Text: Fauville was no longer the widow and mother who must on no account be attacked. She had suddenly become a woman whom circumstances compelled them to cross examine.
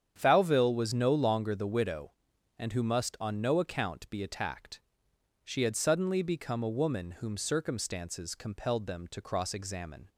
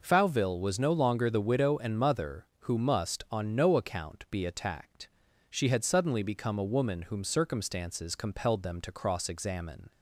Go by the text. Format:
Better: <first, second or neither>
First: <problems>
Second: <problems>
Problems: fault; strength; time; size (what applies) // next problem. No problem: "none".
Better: second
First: starts louder than the rest; strong; until 1.1 s; 8.5 dB // skips "mother"; at 2.7 s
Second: none